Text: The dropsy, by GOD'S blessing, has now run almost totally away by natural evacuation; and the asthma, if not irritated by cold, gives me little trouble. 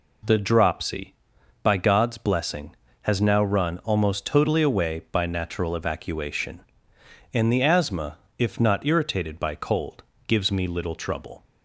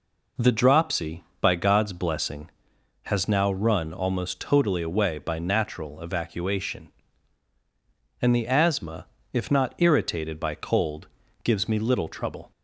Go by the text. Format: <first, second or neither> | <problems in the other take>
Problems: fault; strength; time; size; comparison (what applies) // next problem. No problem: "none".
neither | none